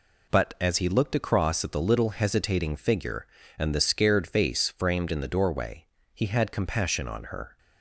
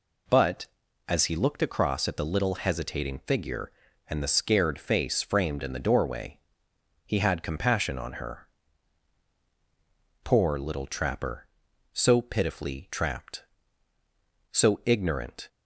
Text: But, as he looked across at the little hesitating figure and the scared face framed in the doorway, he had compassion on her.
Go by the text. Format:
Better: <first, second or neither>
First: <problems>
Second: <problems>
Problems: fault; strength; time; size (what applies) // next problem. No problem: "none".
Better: first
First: none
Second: goes on to say "Poor little trapper so pitifully trapped so ignorant"; strong; from 10.2 s on; 5.2 s long